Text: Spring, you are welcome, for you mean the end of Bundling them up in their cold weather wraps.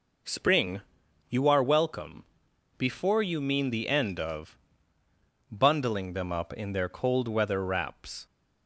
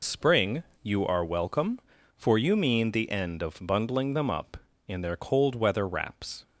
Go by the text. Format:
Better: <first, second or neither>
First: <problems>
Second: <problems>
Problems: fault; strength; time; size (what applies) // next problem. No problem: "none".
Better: second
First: says "before" for "for"; at 2.7 s // pauses between "of" and "Bundling"; noticeable; at 4.5 s; 0.94 s long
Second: none